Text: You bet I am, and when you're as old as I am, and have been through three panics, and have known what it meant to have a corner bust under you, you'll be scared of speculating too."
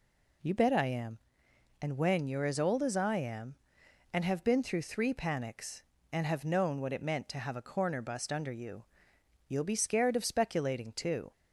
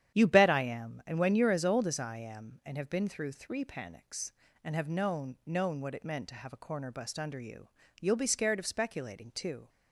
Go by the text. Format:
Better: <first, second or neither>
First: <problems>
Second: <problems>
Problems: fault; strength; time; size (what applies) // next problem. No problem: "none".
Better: first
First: none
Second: starts louder than the rest; strong; until 1.1 s; 9.5 dB // says "known" twice; at 5.4 s